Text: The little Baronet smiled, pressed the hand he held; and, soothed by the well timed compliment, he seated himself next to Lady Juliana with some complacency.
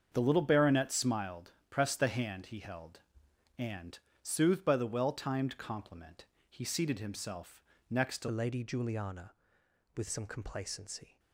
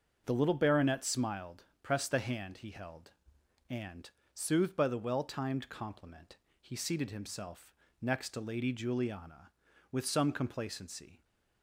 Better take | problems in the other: second | starts louder than the rest; until 1.1 s; 7 dB; also in the second // pauses between "himself" and "next"; slight; at 7.6 s; 0.26 s long; slight in the second // changes voice at "Lady"; from 8.3 s on; 2.8 s long

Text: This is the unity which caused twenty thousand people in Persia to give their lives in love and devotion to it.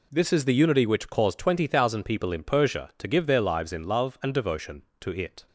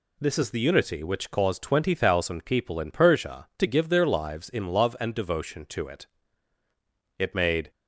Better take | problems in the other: first | goes on to say "It made"; from 7.1 s on; 0.50 s long

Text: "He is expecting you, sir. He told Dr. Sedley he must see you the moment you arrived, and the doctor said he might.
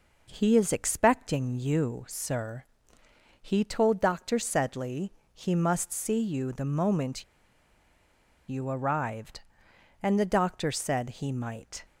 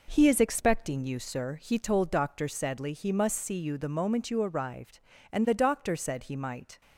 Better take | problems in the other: second | pauses between "Sedley" and "he"; slight; at 5.1 s; 0.24 s long // pauses between "moment" and "you"; strong; at 7.2 s; 1.2 s long

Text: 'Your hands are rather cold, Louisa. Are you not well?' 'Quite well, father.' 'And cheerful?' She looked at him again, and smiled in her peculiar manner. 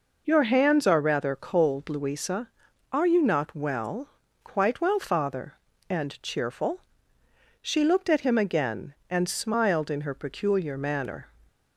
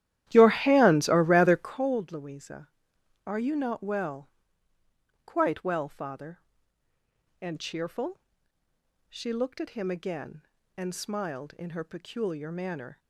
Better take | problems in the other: first | starts louder than the rest; strong; until 1.9 s; 13 dB

